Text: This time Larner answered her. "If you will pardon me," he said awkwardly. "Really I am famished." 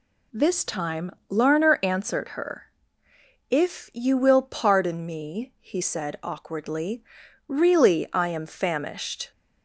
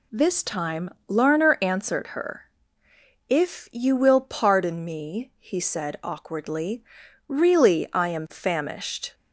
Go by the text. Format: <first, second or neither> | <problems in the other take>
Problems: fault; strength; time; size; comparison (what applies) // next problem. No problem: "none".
neither | pauses between "time" and "Larner"; slight; the same in both